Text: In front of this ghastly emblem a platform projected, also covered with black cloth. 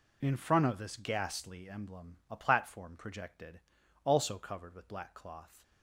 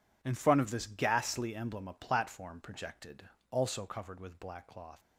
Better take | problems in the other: neither | none

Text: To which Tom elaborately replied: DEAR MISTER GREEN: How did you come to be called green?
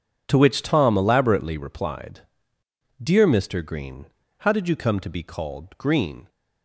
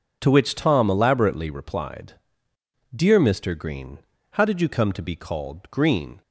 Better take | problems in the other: second | gets quieter; strong; throughout; 15 dB

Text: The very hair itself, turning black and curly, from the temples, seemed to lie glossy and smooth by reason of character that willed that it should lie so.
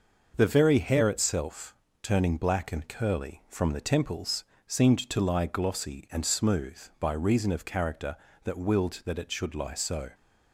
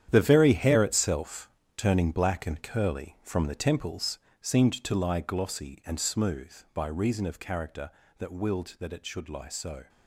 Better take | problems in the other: first | gets quieter; strong; throughout; 11 dB // starts louder than the rest; strong; until 1.1 s; 10 dB; noticeable in the first

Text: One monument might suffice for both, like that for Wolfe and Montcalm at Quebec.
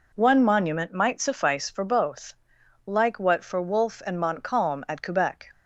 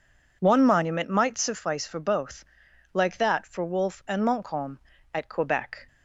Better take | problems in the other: second | says "what" for "that"; at 3.1 s

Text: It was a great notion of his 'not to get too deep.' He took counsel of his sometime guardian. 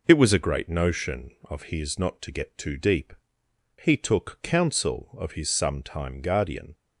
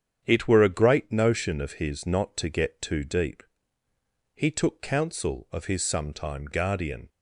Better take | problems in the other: first | starts louder than the rest; strong; until 1.2 s; 8.5 dB // says "were" for "was"; at 0.4 s

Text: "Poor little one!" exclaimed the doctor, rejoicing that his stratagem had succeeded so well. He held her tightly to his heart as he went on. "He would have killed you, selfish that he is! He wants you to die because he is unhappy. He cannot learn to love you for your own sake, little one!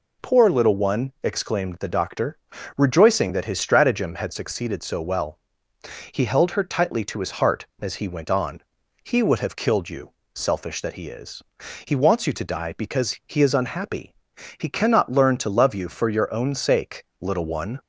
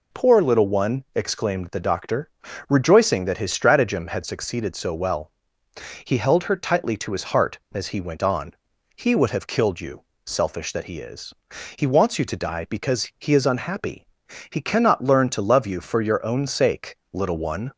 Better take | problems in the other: neither | none

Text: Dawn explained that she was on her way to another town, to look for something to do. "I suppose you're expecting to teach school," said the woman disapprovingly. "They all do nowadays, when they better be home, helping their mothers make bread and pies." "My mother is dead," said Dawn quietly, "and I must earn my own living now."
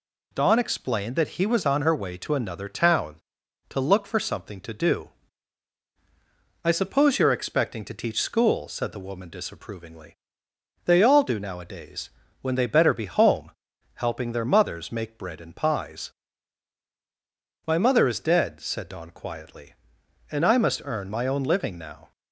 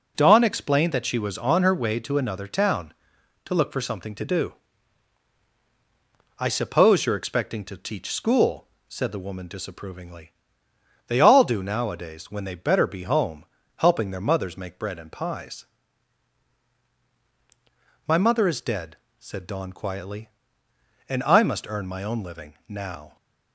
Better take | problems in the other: second | says "he" for "she"; at 1.3 s

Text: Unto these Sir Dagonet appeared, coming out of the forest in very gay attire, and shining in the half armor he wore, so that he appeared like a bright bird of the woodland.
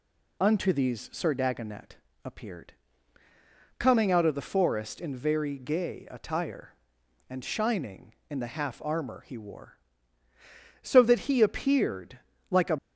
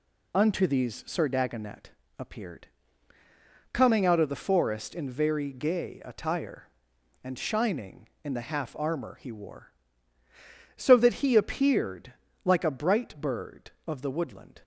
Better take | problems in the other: second | pauses between "Dagonet" and "appeared"; slight; at 1.9 s; 0.28 s long; slight in the second // pauses between "appeared" and "like"; slight; at 12.1 s; 0.32 s long; slight in the second // stops before "bright bird of the woodland"; at 12.7 s

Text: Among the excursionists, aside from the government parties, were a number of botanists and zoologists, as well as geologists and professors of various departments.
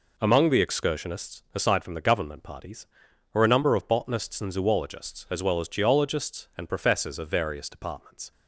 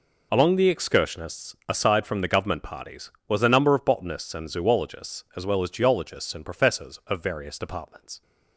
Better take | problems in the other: first | says "was" for "were"; at 3.2 s

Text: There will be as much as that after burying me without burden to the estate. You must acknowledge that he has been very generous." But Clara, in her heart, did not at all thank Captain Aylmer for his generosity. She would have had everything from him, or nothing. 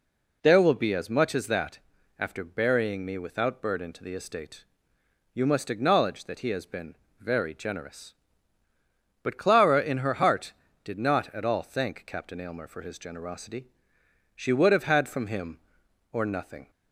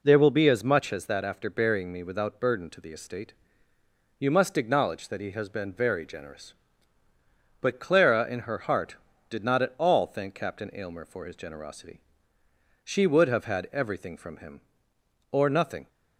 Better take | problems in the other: second | pauses between "that" and "after"; at 1.7 s; 0.38 s long // pauses between "been" and "very"; slight; at 6.9 s; 0.24 s long // skips "everything"; at 15.0 s

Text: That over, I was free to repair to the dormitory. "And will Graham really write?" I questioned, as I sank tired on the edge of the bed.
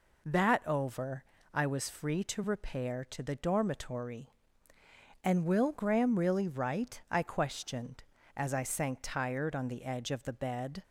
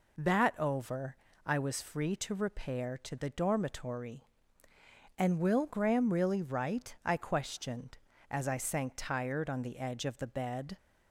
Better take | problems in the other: neither | none

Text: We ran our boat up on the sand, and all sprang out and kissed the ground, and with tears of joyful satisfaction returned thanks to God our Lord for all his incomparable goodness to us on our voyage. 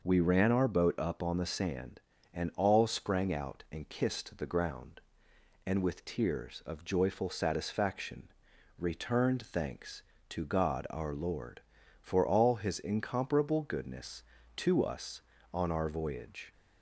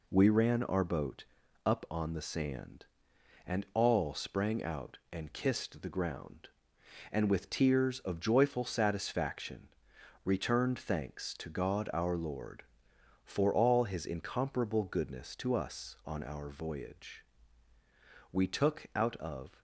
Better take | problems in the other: first | pauses between "boat" and "up"; at 1.2 s; 0.40 s long // pauses between "satisfaction" and "returned"; noticeable; at 9.6 s; 0.56 s long; noticeable in the first // goes on to say "We took out of"; noticeable; from 18.3 s on; 1.3 s long

